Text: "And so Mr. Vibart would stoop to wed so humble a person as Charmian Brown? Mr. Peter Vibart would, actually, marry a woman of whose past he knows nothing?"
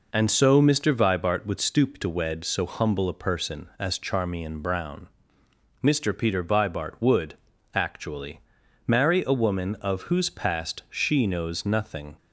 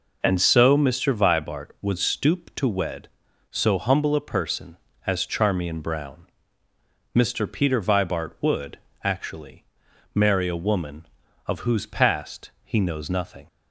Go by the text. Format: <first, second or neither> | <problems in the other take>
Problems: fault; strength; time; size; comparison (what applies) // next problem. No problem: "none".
second | says "she" for "he"; at 10.8 s